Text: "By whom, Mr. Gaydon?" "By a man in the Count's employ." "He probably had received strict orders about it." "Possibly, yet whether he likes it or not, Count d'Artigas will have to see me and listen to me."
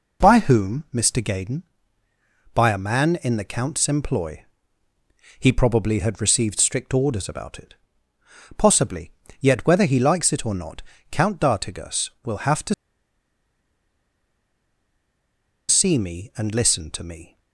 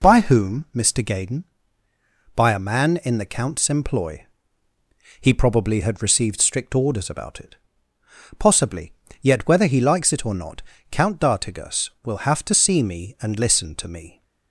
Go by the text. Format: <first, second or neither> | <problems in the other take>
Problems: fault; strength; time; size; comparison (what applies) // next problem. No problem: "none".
second | pauses between "to" and "see"; strong; at 12.7 s; 2.9 s long